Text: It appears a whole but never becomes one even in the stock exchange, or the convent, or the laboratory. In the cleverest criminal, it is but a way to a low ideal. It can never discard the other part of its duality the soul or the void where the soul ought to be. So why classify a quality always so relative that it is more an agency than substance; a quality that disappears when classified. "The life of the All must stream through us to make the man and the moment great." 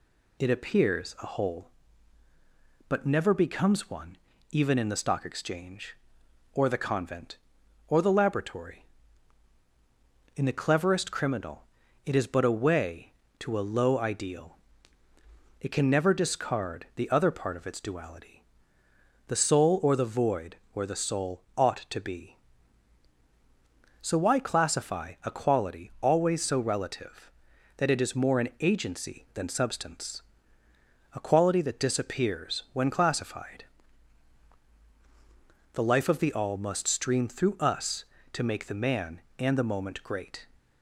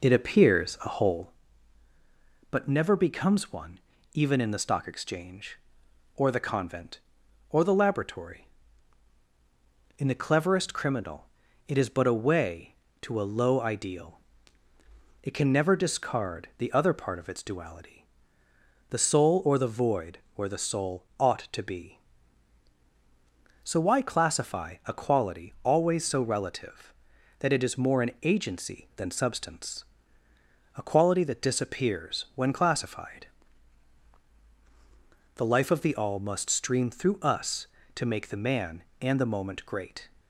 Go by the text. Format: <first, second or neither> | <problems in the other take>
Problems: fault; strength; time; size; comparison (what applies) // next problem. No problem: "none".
first | starts louder than the rest; noticeable; until 1.4 s; 4 dB // pauses between "one" and "even"; slight; at 3.8 s; 0.34 s long; slight in the first // pauses between "duality" and "the"; noticeable; at 18.0 s; 0.84 s long; noticeable in the first // pauses between "void" and "where"; slight; at 20.1 s; 0.18 s long; slight in the first